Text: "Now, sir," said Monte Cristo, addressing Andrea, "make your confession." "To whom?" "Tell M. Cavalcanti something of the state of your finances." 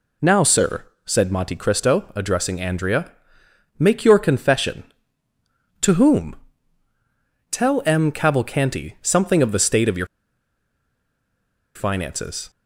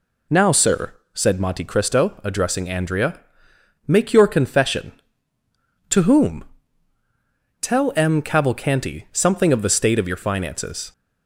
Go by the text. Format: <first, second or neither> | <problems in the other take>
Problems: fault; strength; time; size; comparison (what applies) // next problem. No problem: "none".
second | pauses between "your" and "finances"; strong; at 10.0 s; 1.6 s long